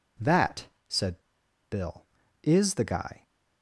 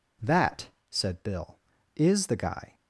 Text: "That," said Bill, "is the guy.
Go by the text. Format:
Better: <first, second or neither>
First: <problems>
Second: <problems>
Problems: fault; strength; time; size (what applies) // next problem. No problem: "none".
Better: second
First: pauses between "said" and "Bill"; noticeable; at 1.2 s; 0.48 s long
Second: none